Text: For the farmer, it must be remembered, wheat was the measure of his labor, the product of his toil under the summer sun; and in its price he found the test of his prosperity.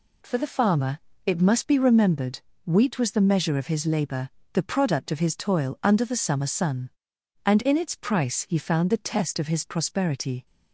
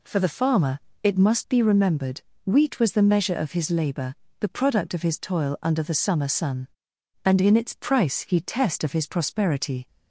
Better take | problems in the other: first | skips "found the"; at 8.4 s

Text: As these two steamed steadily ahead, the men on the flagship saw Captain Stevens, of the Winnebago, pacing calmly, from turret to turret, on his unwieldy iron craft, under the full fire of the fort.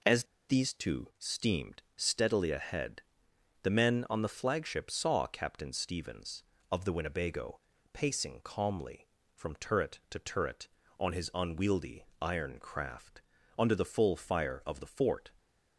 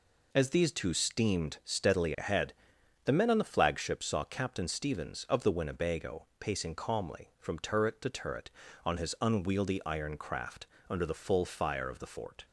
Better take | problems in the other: second | pauses between "As" and "these"; slight; at 0.2 s; 0.23 s long

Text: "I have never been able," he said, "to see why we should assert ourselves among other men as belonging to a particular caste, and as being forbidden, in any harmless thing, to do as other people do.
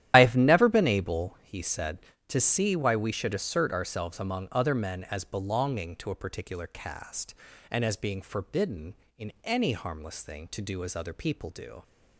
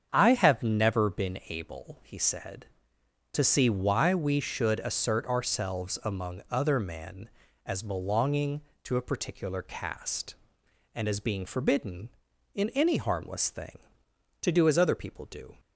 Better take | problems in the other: second | loses the start of "I"; at 0.1 s; 65 ms // starts louder than the rest; strong; until 1.1 s; 11.5 dB; strong in the second

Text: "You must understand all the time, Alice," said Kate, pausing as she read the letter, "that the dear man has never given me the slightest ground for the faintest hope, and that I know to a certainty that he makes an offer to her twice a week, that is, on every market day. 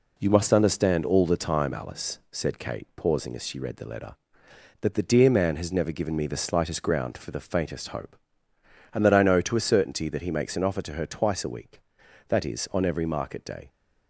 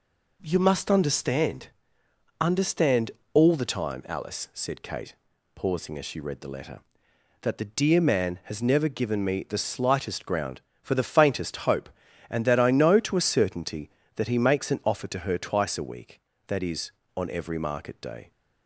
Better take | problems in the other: first | says "understand" twice; at 2.4 s

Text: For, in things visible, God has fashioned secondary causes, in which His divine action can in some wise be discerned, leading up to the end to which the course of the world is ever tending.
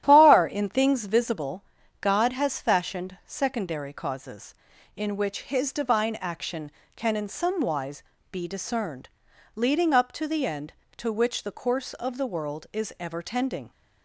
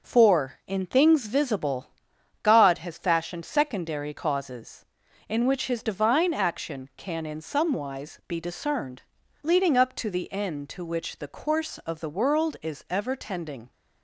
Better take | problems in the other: second | starts louder than the rest; strong; until 1.0 s; 11.5 dB // says "Far" for "For"; at 0.0 s // pauses between "wise" and "be"; slight; at 8.0 s; 0.28 s long

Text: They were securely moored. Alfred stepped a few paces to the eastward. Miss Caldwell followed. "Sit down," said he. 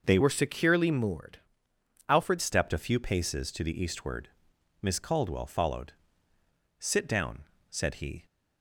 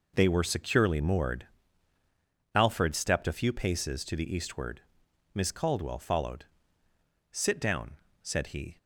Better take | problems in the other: second | changes voice from "were" to "Alfred"; from 0.2 to 2.3 s; 2.1 s long

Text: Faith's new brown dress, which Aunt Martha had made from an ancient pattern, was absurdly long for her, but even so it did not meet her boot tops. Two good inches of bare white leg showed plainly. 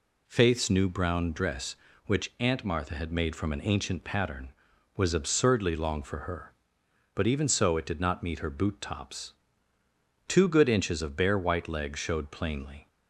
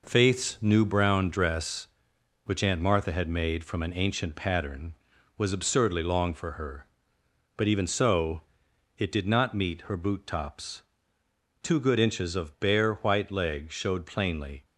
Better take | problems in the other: first | gets quieter; throughout; 6.5 dB // pauses between "so" and "it"; noticeable; at 8.4 s; 0.56 s long

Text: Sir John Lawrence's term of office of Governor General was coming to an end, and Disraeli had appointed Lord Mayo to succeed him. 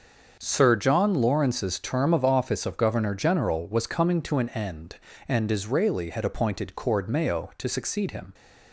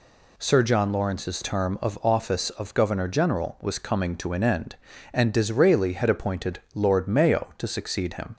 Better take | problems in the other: second | starts louder than the rest; until 1.4 s; 6.5 dB // says "Cord" for "Lord"; at 6.7 s

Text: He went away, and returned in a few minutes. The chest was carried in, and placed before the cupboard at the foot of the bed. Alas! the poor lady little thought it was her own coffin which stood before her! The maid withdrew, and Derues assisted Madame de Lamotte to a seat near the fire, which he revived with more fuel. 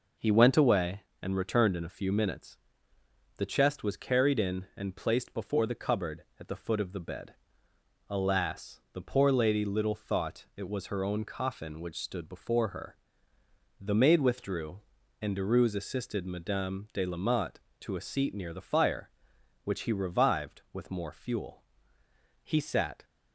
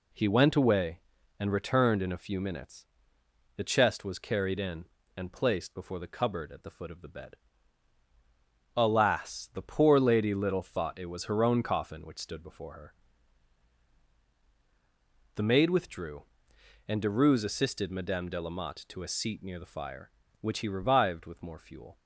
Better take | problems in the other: second | goes on to say "He sat"; noticeable; from 22.4 s on; 0.62 s long

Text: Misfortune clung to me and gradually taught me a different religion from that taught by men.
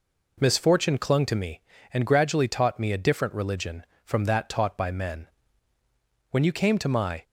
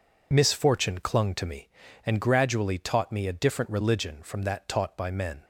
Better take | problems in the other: second | goes on to say "When you came to my"; noticeable; from 6.2 s on; 0.94 s long

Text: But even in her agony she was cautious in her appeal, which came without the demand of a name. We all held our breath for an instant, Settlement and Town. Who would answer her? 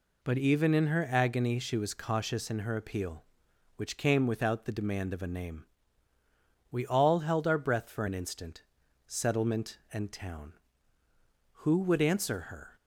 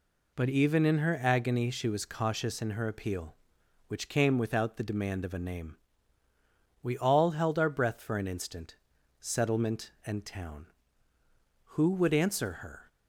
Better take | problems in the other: neither | none

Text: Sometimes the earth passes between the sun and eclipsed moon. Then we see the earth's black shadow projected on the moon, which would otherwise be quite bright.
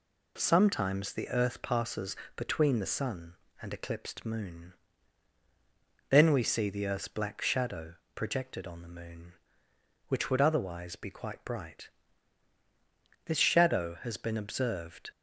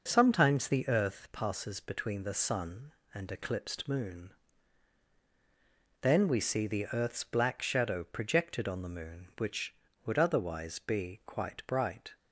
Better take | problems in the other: second | pauses between "passes" and "between"; slight; at 2.1 s; 0.22 s long // pauses between "shadow" and "projected"; slight; at 7.9 s; 0.20 s long // goes on to say "This shadow has been observed"; strong; from 13.2 s on; 1.8 s long

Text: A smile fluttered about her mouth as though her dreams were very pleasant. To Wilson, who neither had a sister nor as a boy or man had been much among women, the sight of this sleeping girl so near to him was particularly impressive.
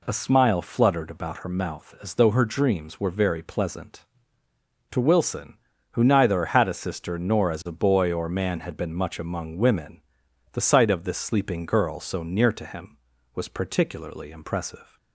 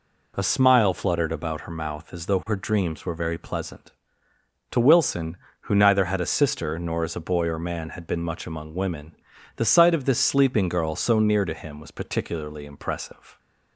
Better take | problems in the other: neither | none

